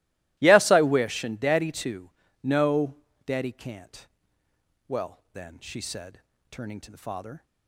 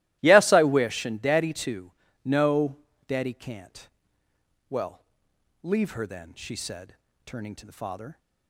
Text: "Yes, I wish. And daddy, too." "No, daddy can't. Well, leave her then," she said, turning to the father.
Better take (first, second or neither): second